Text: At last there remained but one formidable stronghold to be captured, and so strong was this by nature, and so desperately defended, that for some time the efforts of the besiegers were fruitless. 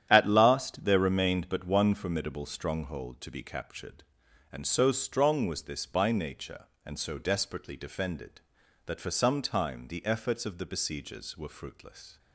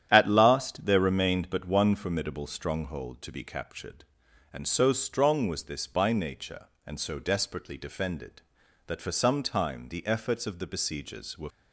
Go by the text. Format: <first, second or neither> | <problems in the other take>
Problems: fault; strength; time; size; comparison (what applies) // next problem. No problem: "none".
first | starts louder than the rest; strong; until 1.1 s; 10.5 dB; strong in the first // stops before "fruitless"; at 11.5 s